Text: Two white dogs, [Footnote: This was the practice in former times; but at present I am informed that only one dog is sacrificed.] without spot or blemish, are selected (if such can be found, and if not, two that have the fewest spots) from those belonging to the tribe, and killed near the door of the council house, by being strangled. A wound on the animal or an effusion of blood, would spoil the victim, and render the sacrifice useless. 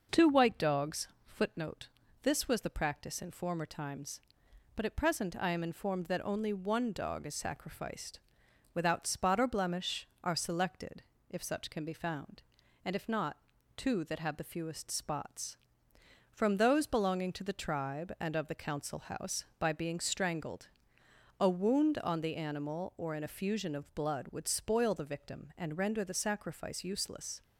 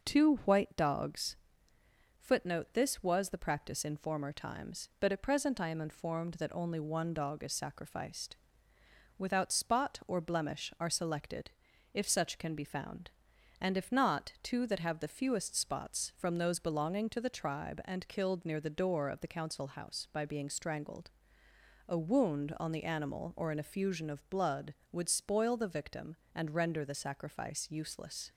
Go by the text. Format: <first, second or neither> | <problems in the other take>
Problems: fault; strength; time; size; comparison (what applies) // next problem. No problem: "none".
second | skips "killed near the door"; at 18.3 s